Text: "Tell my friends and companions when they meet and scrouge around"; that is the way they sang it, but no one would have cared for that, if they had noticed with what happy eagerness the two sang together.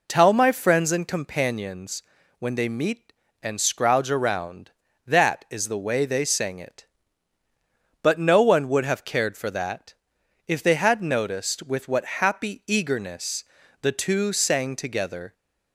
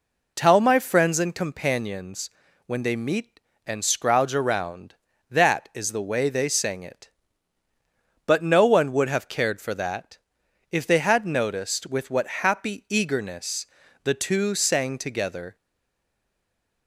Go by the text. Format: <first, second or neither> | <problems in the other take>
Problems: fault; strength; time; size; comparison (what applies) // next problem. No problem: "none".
first | pauses between "companions" and "when"; slight; at 2.2 s; 0.36 s long; slight in the first // pauses between "eagerness" and "the"; at 13.6 s; 0.38 s long; also in the first // stays silent after the last word; noticeable; from 15.5 s on; 1.3 s long